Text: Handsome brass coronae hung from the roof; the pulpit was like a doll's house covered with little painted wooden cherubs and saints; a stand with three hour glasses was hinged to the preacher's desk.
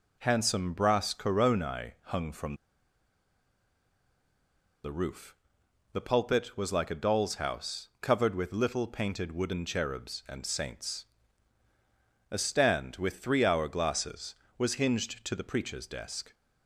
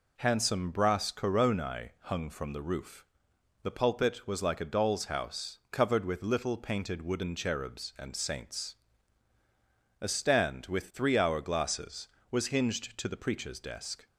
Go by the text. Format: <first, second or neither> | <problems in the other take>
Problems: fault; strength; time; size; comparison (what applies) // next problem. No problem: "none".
second | pauses between "from" and "the"; strong; at 2.5 s; 2.3 s long